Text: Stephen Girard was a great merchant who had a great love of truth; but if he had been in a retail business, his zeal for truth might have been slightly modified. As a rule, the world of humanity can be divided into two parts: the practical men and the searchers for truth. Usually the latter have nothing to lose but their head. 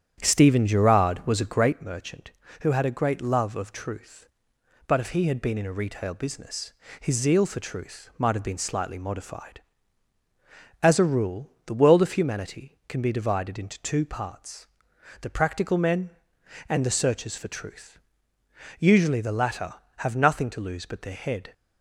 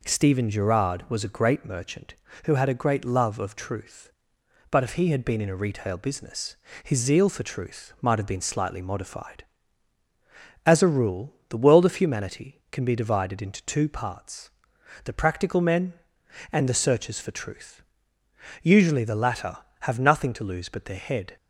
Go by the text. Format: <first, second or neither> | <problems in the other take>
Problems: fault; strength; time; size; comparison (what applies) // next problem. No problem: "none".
second | starts louder than the rest; strong; until 1.7 s; 9 dB